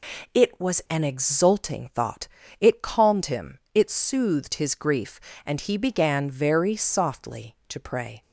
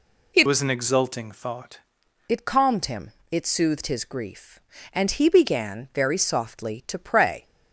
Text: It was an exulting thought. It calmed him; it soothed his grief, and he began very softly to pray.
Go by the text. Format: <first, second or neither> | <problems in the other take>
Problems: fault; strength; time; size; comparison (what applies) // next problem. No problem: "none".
first | changes voice from "was" to "thought"; from 0.4 to 1.7 s; 1.3 s long